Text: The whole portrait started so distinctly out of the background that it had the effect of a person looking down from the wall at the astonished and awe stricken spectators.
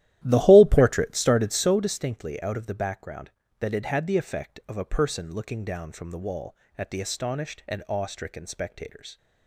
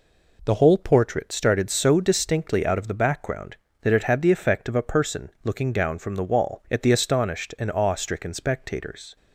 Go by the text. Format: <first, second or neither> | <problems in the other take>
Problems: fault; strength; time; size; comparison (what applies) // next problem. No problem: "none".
second | starts louder than the rest; strong; until 1.9 s; 13.5 dB